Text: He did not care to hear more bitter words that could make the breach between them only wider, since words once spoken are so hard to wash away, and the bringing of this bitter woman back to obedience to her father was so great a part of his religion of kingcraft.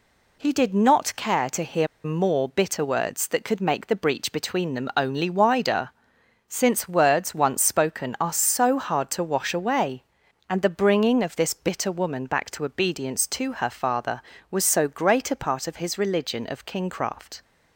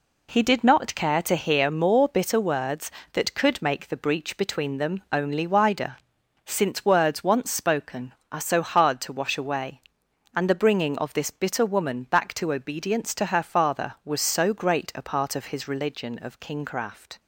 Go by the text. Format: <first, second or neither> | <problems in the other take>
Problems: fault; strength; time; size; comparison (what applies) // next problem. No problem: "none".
second | pauses between "hear" and "more"; slight; at 1.8 s; 0.18 s long